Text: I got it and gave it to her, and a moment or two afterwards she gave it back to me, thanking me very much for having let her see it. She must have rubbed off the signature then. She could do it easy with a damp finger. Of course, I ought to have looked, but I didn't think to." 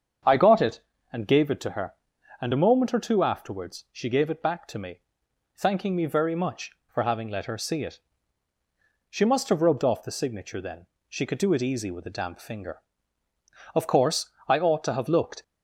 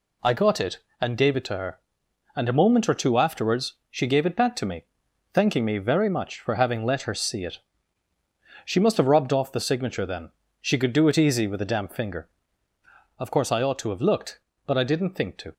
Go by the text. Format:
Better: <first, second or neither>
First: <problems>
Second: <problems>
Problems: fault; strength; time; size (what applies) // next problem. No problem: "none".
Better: second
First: starts louder than the rest; strong; until 1.5 s; 7.5 dB // stops before "but I didn't think to"; at 15.4 s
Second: none